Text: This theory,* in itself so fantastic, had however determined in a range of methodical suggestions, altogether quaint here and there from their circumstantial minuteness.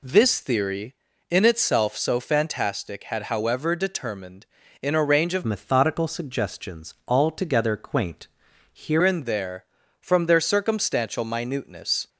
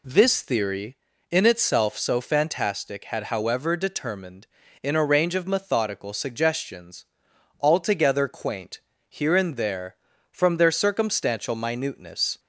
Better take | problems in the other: second | changes voice from "methodical" to "here"; from 5.4 to 9.0 s; 3.6 s long // pauses between "quaint" and "here"; at 8.2 s; 0.44 s long; slight in the second

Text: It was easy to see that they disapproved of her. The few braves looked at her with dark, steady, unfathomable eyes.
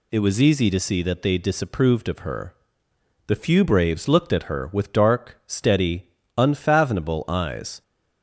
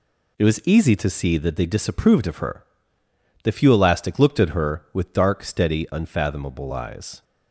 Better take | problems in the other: first | says "elastic" for "braves"; at 3.7 s

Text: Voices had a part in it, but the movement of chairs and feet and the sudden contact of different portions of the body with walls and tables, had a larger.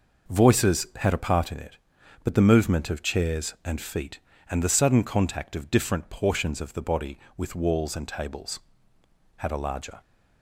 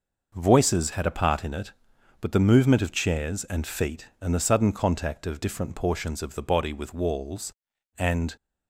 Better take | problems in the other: first | stops before "tables had a larger"; at 8.3 s

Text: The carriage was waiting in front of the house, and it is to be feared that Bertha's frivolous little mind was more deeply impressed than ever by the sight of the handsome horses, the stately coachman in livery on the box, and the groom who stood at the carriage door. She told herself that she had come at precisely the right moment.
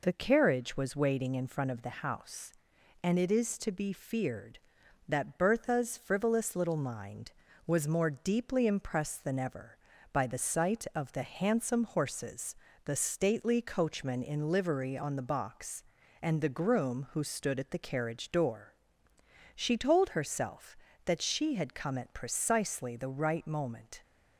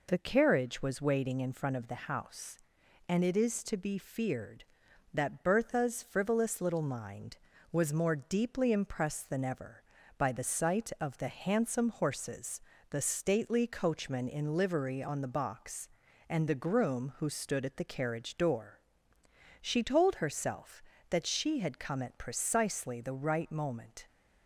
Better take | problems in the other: neither | none

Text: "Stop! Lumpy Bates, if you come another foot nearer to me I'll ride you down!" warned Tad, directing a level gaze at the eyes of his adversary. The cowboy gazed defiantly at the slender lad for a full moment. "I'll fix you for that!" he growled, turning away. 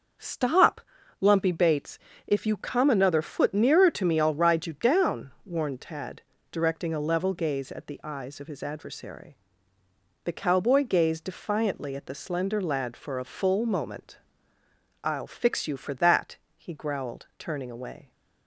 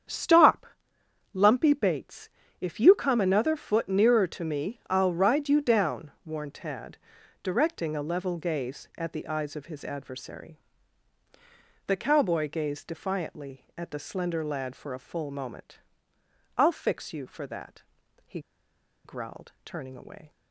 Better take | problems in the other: first | starts louder than the rest; strong; until 1.7 s; 8.5 dB; also in the first // pauses between "he" and "growled"; noticeable; at 18.3 s; 0.65 s long

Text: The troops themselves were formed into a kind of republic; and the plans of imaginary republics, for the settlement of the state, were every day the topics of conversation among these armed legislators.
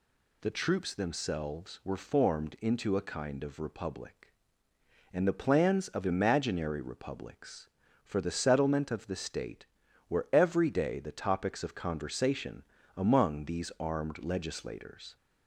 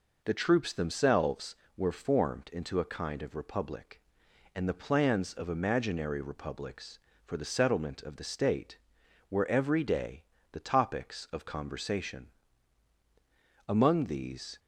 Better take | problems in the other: first | pauses between "day" and "the"; slight; at 10.2 s; 0.26 s long // pauses between "conversation" and "among"; strong; at 12.2 s; 1.4 s long; slight in the first // stops before "armed legislators"; at 14.5 s

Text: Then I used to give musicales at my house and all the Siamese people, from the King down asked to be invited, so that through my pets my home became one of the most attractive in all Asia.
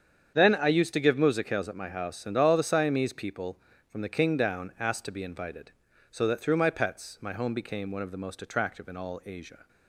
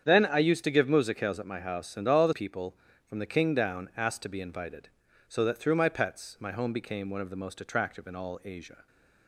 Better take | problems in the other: first | starts louder than the rest; strong; until 1.0 s; 8 dB; strong in the first // skips "Siamese"; at 2.3 s

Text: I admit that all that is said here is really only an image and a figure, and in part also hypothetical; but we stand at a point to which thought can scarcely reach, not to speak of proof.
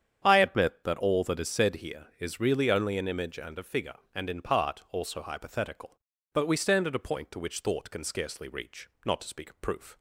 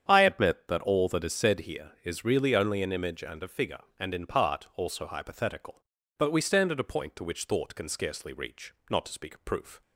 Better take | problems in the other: neither | starts louder than the rest; strong; the same in both

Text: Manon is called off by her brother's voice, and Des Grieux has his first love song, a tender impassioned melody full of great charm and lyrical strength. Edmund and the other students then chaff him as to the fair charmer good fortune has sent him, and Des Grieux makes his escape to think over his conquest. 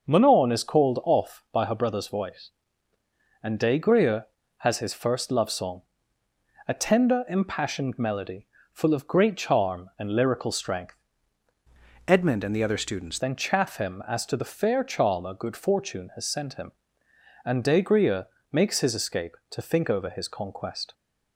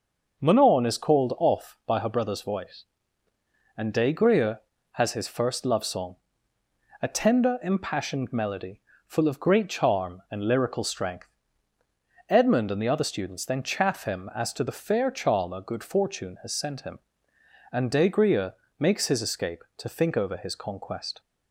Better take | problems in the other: second | starts louder than the rest; noticeable; until 1.1 s; 6 dB // pauses between "melody" and "full"; slight; at 8.4 s; 0.28 s long; slight in the second // changes voice from "Edmund" to "students"; from 12.0 to 13.1 s; 1.1 s long // pauses between "Grieux" and "makes"; slight; at 18.2 s; 0.26 s long; slight in the second

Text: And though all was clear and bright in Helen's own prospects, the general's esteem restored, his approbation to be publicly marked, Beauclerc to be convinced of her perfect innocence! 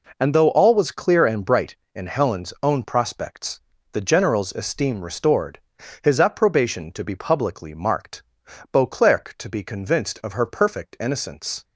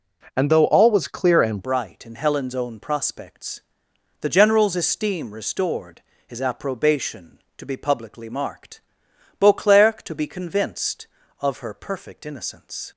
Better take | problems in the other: first | changes voice at "bright"; from 1.6 s on; 11.3 s long

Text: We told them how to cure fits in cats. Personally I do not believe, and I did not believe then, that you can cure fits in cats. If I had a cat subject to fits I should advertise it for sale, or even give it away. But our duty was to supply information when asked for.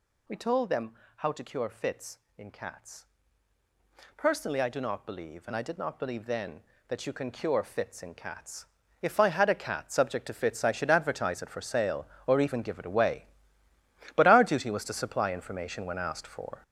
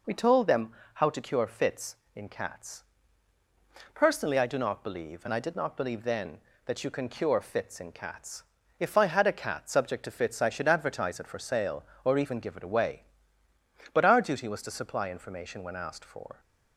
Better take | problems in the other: second | gets louder; strong; throughout; 8 dB // pauses between "them" and "how"; slight; at 0.9 s; 0.24 s long; slight in the second

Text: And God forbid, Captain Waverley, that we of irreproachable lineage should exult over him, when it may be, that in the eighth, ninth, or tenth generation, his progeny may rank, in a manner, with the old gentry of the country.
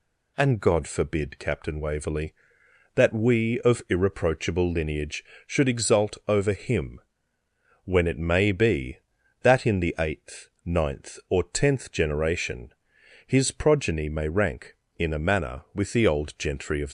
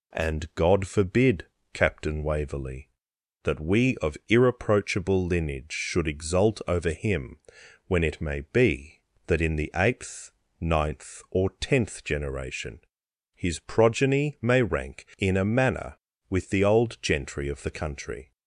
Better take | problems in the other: second | stops before "the country"; at 16.8 s

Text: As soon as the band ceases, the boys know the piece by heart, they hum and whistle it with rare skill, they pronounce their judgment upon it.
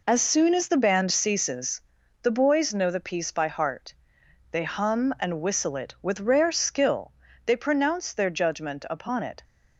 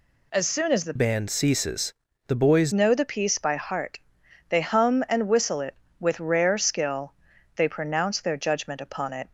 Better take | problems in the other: first | changes voice from "band" to "boys"; from 0.9 to 2.7 s; 1.8 s long

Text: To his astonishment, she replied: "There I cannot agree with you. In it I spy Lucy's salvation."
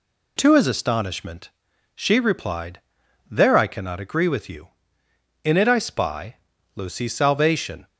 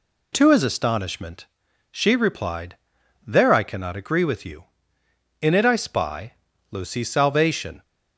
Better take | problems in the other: neither | pauses between "spy" and "Lucy's"; the same in both

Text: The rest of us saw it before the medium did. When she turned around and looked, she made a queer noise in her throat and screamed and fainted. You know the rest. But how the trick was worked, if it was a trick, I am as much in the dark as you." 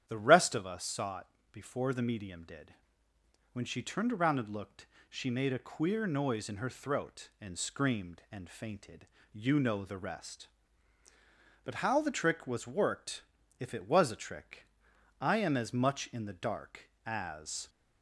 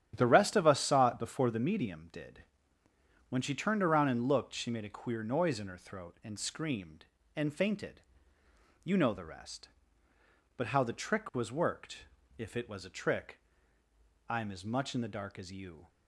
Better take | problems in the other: second | starts louder than the rest; strong; until 1.1 s; 9.5 dB; strong in the second // pauses between "it" and "before"; slight; at 1.2 s; 0.24 s long // stops before "you"; at 17.6 s

